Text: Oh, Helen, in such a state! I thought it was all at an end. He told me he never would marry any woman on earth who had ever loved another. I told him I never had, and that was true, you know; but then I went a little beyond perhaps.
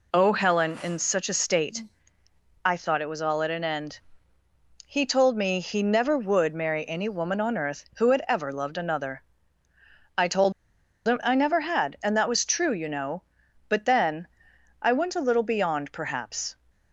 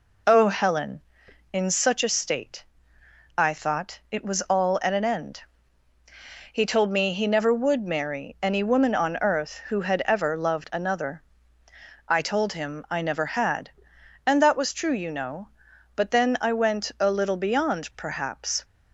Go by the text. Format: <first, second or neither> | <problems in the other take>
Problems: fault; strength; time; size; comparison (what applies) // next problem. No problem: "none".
second | pauses between "told" and "him"; noticeable; at 10.5 s; 0.53 s long // pauses between "then" and "I"; noticeable; at 14.2 s; 0.56 s long